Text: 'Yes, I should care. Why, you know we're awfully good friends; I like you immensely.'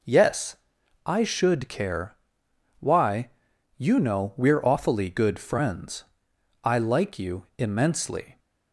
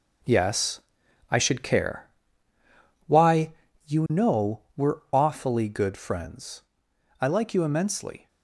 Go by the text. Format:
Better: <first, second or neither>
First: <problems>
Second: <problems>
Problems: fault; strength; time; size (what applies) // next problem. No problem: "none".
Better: first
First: none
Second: gets quieter; strong; throughout; 8 dB